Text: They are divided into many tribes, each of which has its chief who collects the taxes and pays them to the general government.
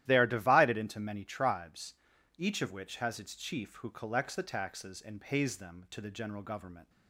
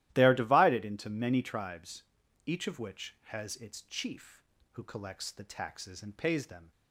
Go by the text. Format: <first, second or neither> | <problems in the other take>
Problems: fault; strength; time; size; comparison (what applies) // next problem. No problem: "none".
first | starts louder than the rest; strong; until 1.1 s; 14.5 dB; strong in the first // stops before "to the general government"; at 6.7 s